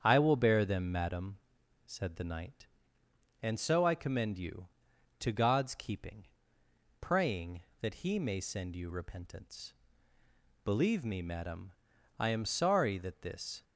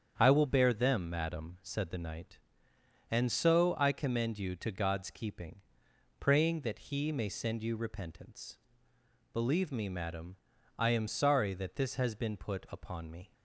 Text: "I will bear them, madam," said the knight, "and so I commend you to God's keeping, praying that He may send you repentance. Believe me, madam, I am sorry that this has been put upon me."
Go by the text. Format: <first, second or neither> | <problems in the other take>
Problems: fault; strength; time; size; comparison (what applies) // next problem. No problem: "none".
second | starts louder than the rest; strong; until 1.0 s; 8 dB; strong in the second // stops before "has been put upon me"; at 13.6 s